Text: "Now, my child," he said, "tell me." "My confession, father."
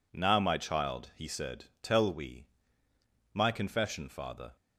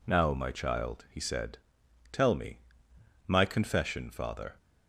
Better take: second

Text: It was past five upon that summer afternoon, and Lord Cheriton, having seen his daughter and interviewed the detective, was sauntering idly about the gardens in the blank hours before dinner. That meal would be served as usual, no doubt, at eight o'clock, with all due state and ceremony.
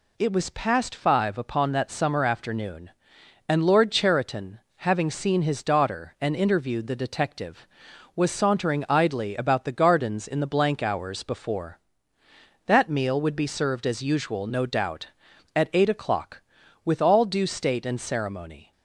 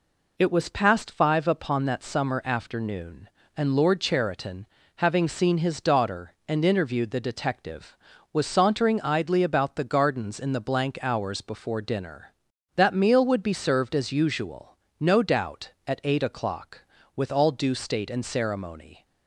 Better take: second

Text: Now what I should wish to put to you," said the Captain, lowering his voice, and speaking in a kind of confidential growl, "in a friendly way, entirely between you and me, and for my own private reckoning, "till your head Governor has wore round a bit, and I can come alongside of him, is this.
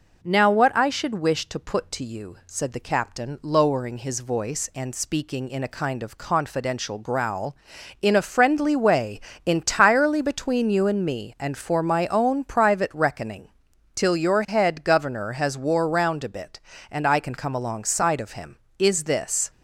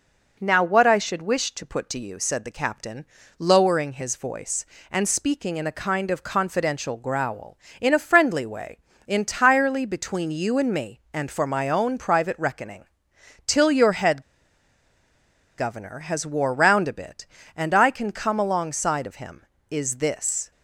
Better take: first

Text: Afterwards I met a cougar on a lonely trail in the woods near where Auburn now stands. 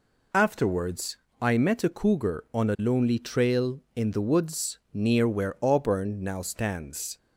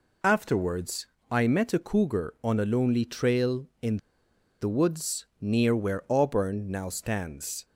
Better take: first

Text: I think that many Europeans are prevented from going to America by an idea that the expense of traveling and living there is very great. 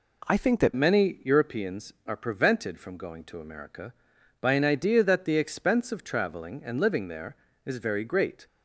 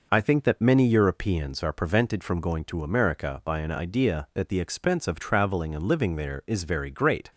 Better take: second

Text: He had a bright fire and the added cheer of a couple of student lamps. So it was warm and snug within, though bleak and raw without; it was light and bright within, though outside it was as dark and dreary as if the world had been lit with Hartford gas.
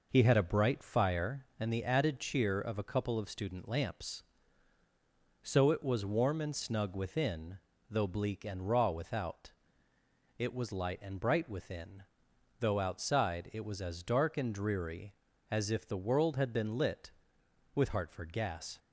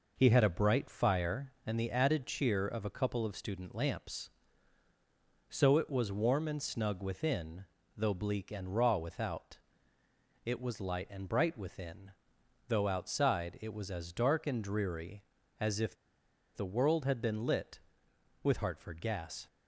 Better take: first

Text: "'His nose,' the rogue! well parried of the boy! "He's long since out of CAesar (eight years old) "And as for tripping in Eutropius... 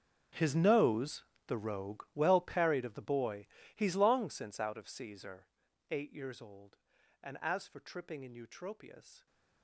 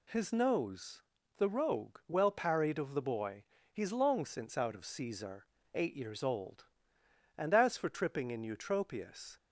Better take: second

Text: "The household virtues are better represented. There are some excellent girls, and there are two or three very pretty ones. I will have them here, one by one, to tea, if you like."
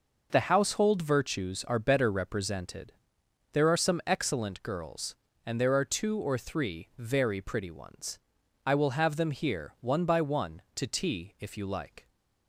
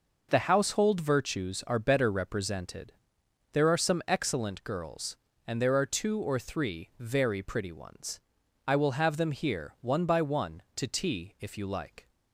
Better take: neither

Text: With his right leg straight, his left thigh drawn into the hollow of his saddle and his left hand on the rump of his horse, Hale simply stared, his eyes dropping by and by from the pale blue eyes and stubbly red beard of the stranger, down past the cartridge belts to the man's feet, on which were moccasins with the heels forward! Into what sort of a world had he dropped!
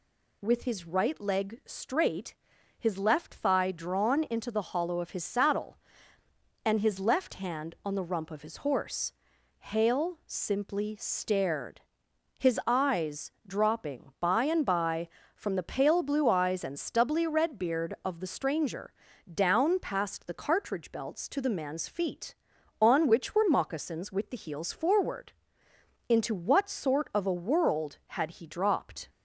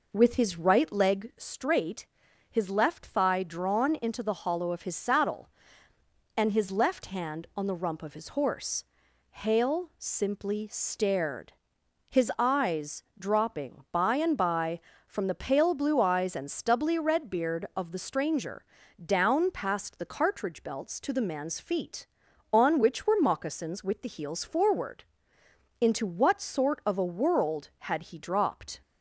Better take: first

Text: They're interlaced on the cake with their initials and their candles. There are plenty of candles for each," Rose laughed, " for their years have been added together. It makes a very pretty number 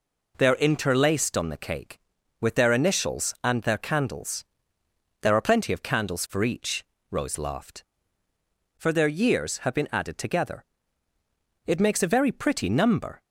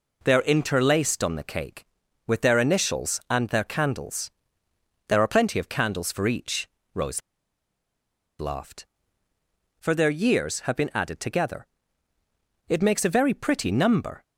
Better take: first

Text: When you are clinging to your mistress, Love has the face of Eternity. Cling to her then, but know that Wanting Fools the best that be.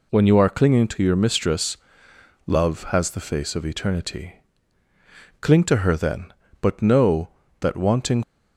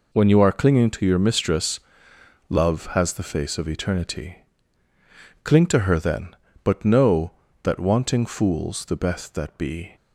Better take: second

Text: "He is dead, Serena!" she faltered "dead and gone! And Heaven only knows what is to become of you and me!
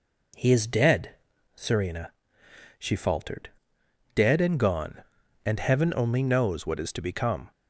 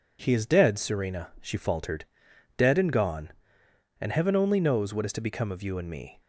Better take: second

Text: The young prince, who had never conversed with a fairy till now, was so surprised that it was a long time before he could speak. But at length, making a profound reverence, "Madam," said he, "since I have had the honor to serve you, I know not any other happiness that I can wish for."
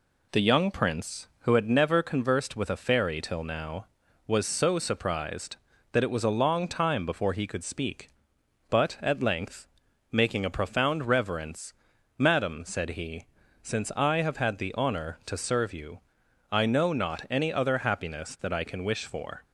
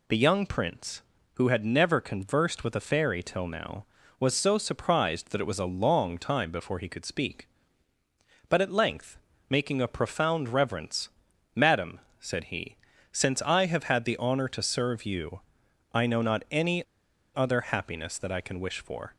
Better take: first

